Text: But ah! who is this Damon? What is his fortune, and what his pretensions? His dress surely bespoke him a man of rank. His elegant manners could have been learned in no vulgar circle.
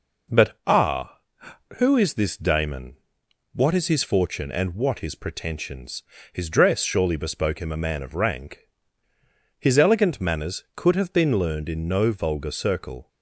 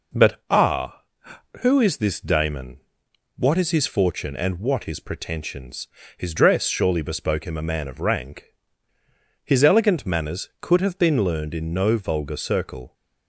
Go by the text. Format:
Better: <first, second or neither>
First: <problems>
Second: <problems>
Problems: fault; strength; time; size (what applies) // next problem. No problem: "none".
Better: neither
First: none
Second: none